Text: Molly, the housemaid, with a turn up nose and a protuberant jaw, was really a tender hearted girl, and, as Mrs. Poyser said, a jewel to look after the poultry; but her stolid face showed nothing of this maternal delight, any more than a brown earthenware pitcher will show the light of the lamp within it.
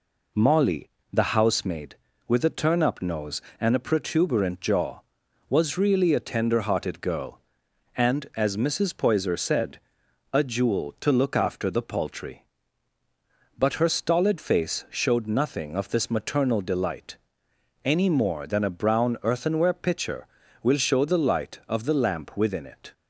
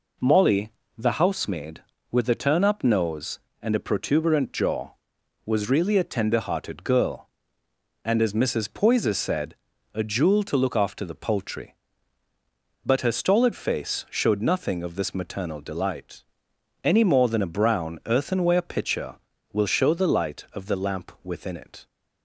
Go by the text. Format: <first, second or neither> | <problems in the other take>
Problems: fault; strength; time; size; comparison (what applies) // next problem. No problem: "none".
neither | none